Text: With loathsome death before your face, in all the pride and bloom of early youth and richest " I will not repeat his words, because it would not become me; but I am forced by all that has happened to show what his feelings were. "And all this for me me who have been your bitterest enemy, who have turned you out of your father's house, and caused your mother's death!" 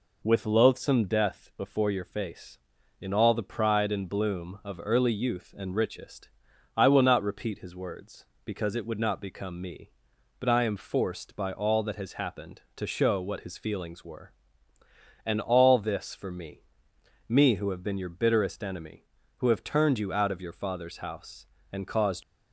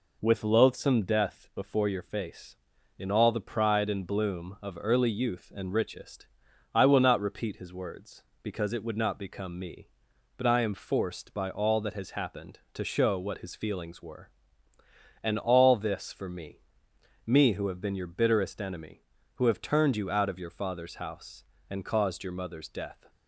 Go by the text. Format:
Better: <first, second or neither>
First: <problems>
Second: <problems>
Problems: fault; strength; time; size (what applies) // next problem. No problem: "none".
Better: second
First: pauses between "me" and "me"; noticeable; at 16.6 s; 0.66 s long // stops before "your mother's death"; at 22.2 s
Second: pauses between "me" and "me"; noticeable; at 16.5 s; 0.66 s long